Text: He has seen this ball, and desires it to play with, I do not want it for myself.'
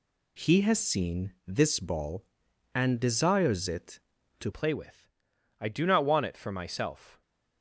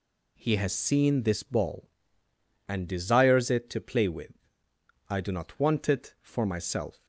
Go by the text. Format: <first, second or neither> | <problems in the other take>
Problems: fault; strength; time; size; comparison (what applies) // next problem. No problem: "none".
second | changes voice at "play"; from 4.5 s on; 2.7 s long